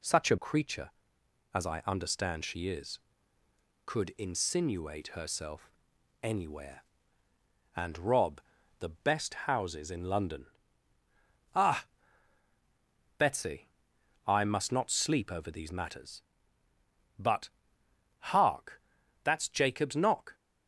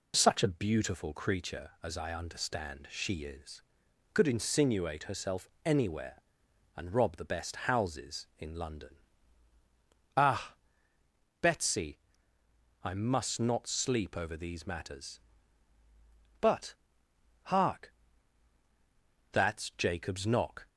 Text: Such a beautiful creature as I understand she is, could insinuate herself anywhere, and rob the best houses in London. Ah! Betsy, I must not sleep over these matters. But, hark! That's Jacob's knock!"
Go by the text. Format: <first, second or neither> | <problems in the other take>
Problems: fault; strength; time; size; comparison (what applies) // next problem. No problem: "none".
second | skips "beautiful"; at 0.3 s // pauses between "herself" and "anywhere"; noticeable; at 5.6 s; 0.54 s long; slight in the second // pauses between "rob" and "the"; at 8.3 s; 0.40 s long